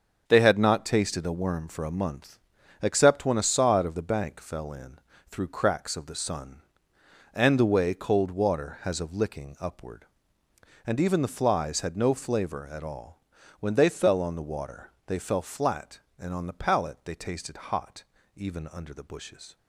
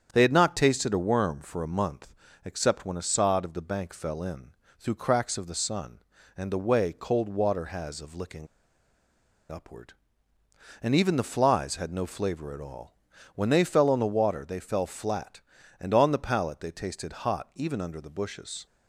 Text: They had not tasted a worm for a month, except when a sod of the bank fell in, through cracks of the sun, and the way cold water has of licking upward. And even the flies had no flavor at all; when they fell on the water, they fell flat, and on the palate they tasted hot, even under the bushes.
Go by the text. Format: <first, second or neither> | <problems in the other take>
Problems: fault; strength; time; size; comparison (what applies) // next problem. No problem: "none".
first | starts louder than the rest; strong; until 1.1 s; 7.5 dB; also in the first // pauses between "licking" and "upward"; at 8.4 s; 1.0 s long